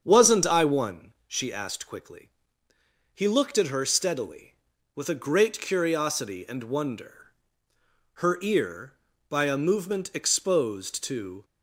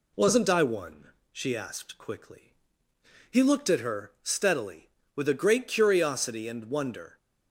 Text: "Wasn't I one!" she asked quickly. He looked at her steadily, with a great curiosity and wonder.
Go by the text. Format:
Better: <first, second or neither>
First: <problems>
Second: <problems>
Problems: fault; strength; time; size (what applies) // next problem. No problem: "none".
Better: second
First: starts louder than the rest; strong; until 1.0 s; 7.5 dB // goes on to say "Her ear by a movement exposed to"; strong; from 8.1 s on; 3.3 s long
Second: none